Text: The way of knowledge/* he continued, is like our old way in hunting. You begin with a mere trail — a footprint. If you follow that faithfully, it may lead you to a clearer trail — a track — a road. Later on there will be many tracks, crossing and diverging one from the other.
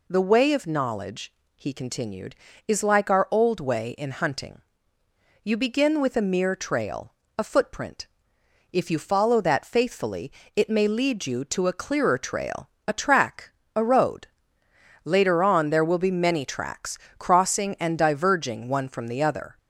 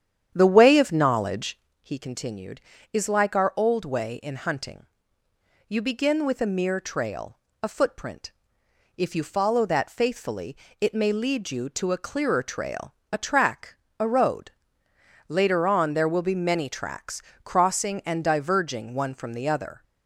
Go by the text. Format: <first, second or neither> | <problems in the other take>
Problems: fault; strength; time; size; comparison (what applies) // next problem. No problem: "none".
first | starts louder than the rest; strong; until 1.7 s; 9 dB